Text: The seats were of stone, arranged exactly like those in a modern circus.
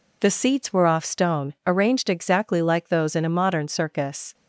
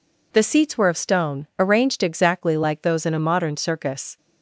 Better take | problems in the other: second | says "off" for "of"; at 0.8 s

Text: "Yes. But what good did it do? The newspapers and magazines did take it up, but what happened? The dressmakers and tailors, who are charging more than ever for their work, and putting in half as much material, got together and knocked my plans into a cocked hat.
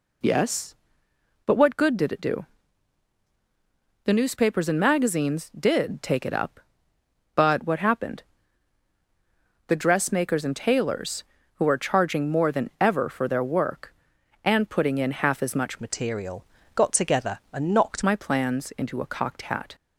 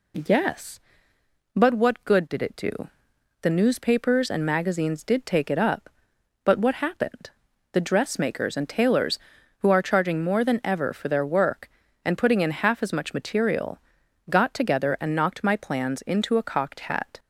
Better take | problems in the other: second | changes voice from "material" to "knocked"; from 15.7 to 18.0 s; 2.3 s long

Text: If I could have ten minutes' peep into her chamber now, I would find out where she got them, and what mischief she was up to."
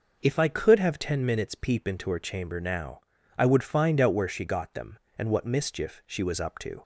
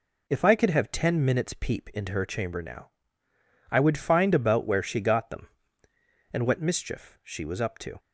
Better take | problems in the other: first | says "about" for "out"; at 4.3 s

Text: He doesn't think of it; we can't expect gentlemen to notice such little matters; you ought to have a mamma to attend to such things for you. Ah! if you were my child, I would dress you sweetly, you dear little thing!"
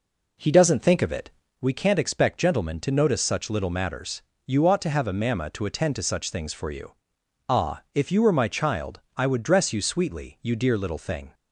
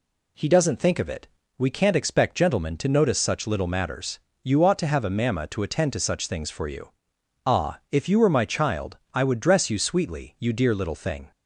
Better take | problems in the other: second | starts louder than the rest; noticeable; until 1.7 s; 4 dB

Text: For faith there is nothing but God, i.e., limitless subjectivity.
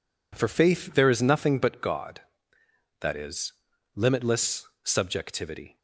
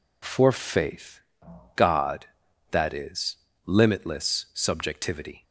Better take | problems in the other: first | skips "there is nothing but"; at 1.4 s

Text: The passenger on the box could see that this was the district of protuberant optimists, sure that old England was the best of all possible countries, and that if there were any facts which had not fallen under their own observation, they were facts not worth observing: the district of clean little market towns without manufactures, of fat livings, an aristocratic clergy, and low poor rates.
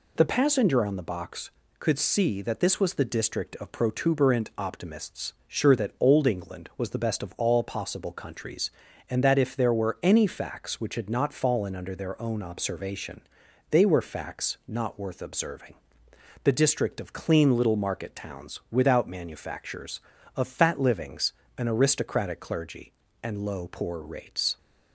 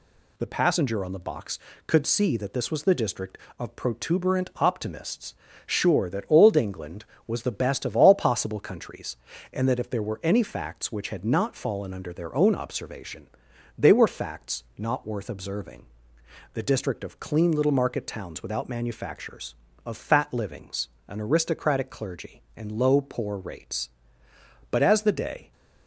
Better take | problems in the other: first | goes on to say "But as the day"; noticeable; from 24.6 s on; 0.82 s long

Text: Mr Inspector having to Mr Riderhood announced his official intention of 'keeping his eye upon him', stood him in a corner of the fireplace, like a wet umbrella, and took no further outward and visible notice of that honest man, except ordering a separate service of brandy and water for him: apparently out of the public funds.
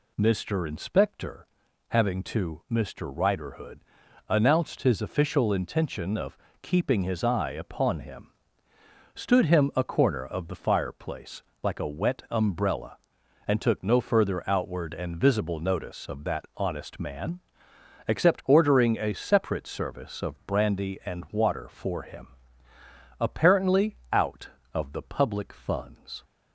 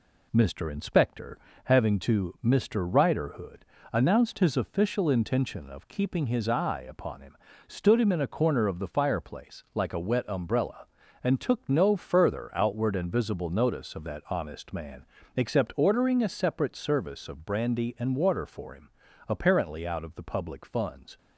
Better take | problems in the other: second | pauses between "Inspector" and "having"; at 1.4 s; 0.42 s long; slight in the second // pauses between "Riderhood" and "announced"; noticeable; at 3.7 s; 0.48 s long; slight in the second // pauses between "of" and "keeping"; slight; at 6.3 s; 0.24 s long // skips "in"; at 9.7 s // pauses between "apparently" and "out"; slight; at 23.9 s; 0.16 s long

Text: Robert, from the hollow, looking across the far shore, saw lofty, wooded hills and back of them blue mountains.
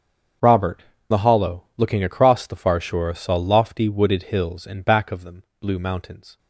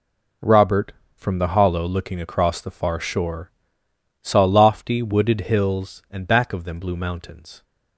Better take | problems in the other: second | starts louder than the rest; strong; until 1.8 s; 7 dB // skips "from"; at 0.9 s // pauses between "them" and "blue"; slight; at 5.4 s; 0.18 s long

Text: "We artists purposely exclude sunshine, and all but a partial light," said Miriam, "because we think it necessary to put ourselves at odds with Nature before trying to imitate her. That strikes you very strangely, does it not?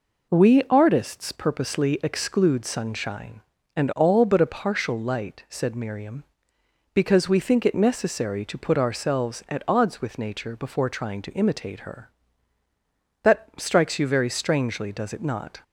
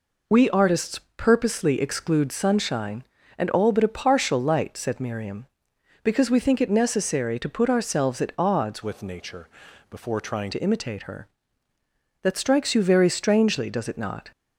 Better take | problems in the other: first | pauses between "artists" and "purposely"; slight; at 0.9 s; 0.18 s long // changes voice from "with" to "trying"; from 8.8 to 10.4 s; 1.6 s long // pauses between "Nature" and "before"; at 9.4 s; 0.44 s long

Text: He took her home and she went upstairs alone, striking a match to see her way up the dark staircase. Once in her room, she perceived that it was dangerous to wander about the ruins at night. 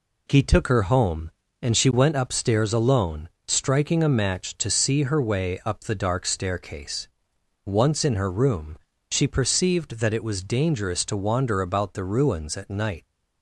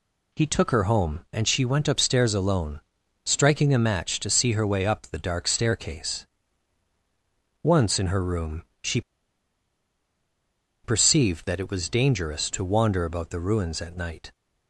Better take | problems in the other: first | pauses between "she" and "perceived"; strong; at 9.0 s; 1.8 s long

